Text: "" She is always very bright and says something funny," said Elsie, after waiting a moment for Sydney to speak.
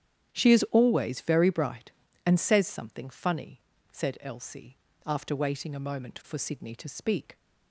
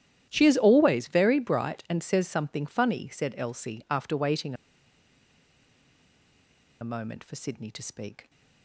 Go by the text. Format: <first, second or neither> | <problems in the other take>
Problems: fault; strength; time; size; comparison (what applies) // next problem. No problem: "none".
first | starts louder than the rest; strong; until 1.2 s; 11.5 dB; strong in the first // pauses between "waiting" and "a"; strong; at 4.5 s; 2.2 s long